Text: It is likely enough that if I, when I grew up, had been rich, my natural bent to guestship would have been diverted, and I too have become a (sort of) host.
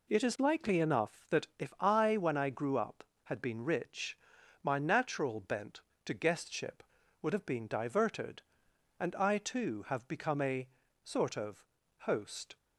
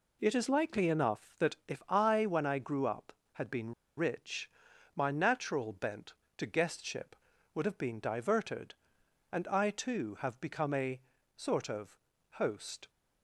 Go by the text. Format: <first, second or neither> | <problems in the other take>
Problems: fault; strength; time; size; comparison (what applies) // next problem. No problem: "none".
first | pauses between "been" and "rich"; slight; at 3.7 s; 0.25 s long